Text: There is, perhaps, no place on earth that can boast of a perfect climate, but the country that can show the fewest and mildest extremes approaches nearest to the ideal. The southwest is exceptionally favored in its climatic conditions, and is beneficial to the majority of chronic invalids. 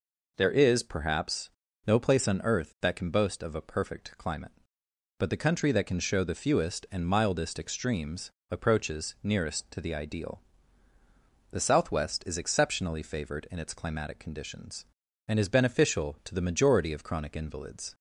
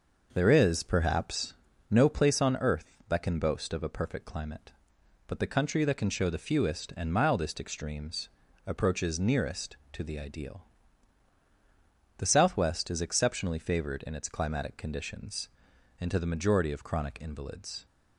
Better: first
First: pauses between "extremes" and "approaches"; slight; at 8.3 s; 0.18 s long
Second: pauses between "extremes" and "approaches"; slight; at 8.2 s; 0.36 s long // skips "is beneficial"; at 16.1 s

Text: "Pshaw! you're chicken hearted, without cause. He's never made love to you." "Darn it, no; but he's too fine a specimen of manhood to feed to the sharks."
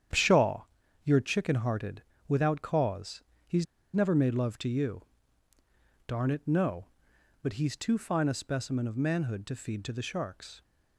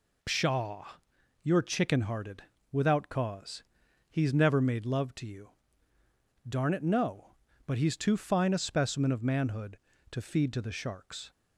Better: second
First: starts louder than the rest; strong; until 1.5 s; 9 dB // pauses between "He's" and "never"; slight; at 3.6 s; 0.28 s long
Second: none

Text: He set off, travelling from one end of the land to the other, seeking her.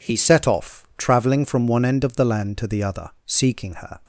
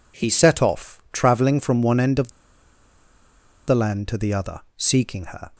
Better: first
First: none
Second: pauses between "of" and "the"; strong; at 2.3 s; 1.3 s long

